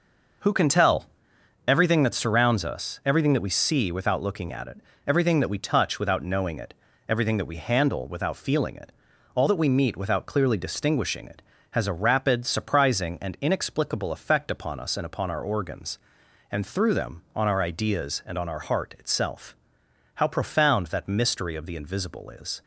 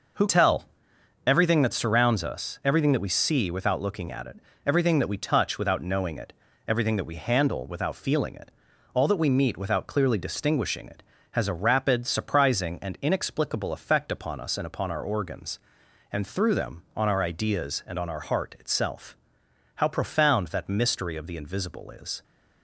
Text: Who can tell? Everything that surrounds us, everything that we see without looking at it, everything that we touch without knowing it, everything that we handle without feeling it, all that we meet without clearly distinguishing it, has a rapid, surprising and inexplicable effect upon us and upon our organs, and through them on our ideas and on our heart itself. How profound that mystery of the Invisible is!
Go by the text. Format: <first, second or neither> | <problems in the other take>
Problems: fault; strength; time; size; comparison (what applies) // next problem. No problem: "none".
first | skips "can"; at 0.2 s